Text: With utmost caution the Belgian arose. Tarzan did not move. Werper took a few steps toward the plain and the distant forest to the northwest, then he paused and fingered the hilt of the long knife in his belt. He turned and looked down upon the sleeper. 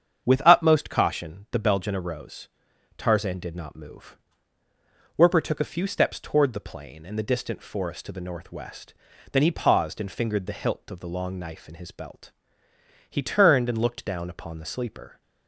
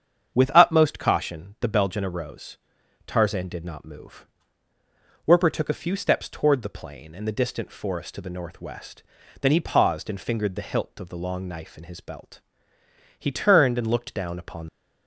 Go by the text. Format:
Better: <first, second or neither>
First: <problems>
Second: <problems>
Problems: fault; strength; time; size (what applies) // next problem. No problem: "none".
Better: first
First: starts louder than the rest; strong; until 1.2 s; 8 dB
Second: starts louder than the rest; strong; until 1.3 s; 8 dB // stops before "the sleeper"; at 14.6 s